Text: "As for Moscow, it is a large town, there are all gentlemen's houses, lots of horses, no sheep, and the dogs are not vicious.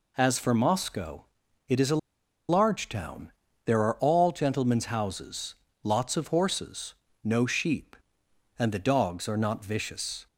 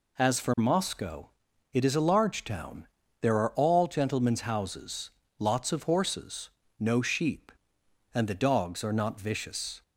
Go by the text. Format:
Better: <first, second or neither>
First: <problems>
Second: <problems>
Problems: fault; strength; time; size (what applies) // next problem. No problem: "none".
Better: second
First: pauses between "a" and "large"; noticeable; at 1.9 s; 0.50 s long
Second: none